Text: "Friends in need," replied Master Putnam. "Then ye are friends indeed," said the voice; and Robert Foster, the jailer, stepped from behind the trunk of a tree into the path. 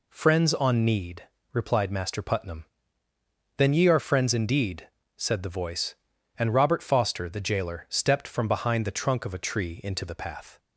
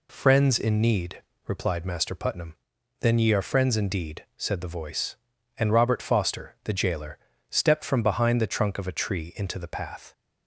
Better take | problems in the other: second | says "on" for "in"; at 0.5 s

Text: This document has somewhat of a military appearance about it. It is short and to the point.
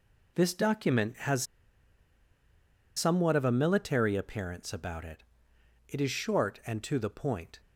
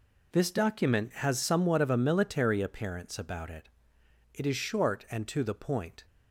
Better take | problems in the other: second | pauses between "has" and "somewhat"; strong; at 1.4 s; 1.5 s long

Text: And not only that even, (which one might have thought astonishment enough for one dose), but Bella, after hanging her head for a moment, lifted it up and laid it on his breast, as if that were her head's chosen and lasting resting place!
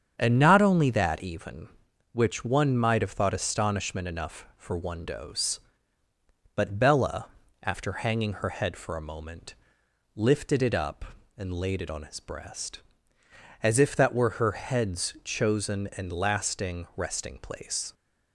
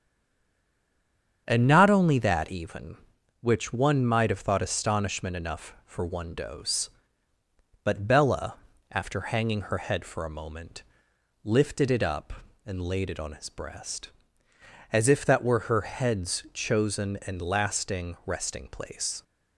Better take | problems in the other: first | stays silent before the first word; noticeable; until 1.4 s; 1.4 s long // starts louder than the rest; strong; until 2.4 s; 8 dB; strong in the first

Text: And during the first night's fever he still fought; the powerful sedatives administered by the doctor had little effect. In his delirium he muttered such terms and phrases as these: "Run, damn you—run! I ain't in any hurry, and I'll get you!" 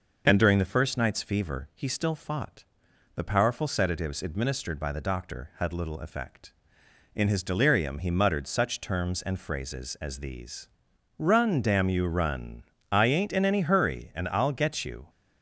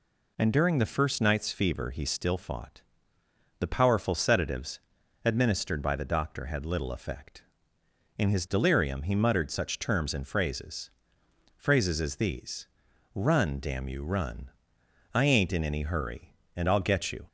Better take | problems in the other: first | pauses between "sedatives" and "administered"; at 4.8 s; 0.44 s long // says "phrases" twice; at 11.5 s

